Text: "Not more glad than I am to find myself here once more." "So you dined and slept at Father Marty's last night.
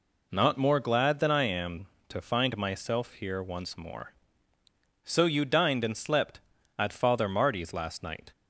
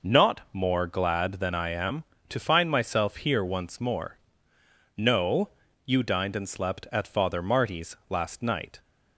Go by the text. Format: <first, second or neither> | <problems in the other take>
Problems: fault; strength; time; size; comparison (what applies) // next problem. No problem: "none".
first | says "No" for "So"; at 4.9 s